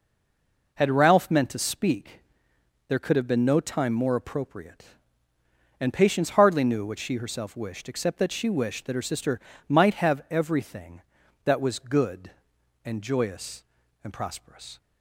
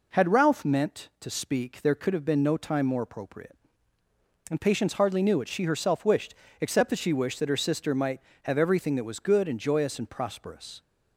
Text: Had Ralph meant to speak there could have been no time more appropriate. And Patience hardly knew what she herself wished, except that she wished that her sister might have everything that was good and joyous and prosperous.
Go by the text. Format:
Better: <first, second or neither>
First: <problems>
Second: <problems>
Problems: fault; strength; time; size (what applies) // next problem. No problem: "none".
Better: second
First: stays silent before the first word; slight; until 0.7 s; 0.7 s long // pauses between "speak" and "there"; noticeable; at 2.2 s; 0.68 s long // pauses between "sister" and "might"; slight; at 9.4 s; 0.26 s long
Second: none